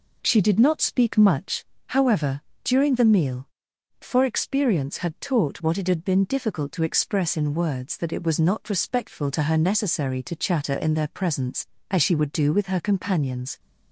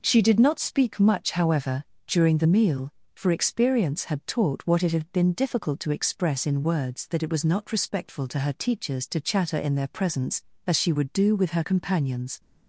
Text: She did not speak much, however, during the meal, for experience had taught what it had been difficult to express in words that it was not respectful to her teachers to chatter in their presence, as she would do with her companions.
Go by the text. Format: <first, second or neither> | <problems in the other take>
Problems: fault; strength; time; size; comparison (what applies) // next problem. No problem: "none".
second | says "necessary" for "teachers"; at 9.5 s